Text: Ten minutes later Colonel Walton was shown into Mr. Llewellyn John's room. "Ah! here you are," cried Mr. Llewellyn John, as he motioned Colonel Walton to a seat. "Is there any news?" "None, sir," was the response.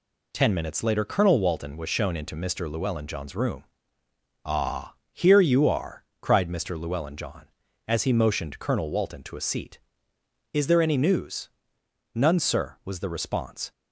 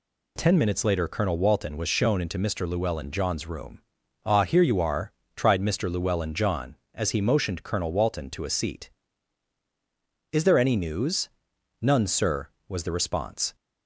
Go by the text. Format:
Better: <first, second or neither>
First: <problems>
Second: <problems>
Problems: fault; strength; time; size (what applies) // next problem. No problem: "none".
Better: first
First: none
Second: says "tried" for "cried"; at 5.3 s